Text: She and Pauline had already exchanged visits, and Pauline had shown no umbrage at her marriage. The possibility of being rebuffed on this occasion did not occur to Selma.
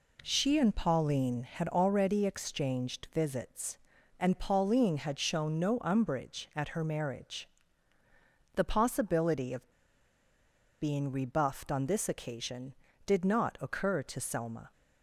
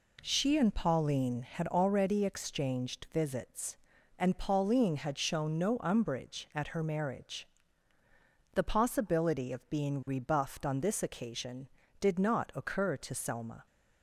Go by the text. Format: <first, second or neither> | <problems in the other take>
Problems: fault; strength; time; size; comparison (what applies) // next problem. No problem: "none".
second | pauses between "of" and "being"; at 9.7 s; 1.1 s long